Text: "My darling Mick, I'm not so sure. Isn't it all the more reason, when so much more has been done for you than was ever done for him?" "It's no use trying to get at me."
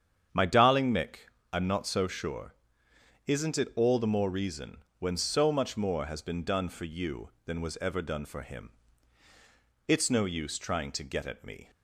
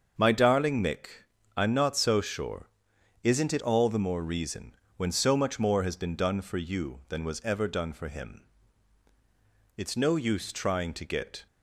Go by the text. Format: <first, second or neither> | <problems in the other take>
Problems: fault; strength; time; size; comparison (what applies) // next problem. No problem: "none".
first | starts louder than the rest; until 1.6 s; 7 dB; strong in the first // stops before "at me"; at 11.4 s